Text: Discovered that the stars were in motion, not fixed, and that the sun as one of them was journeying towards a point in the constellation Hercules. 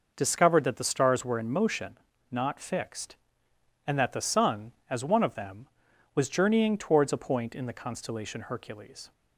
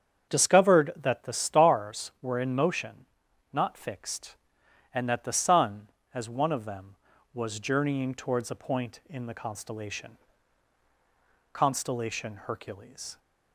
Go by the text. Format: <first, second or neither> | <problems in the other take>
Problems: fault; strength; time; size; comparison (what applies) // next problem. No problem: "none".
first | starts louder than the rest; strong; until 1.3 s; 8 dB // says "constellation" twice; at 11.5 s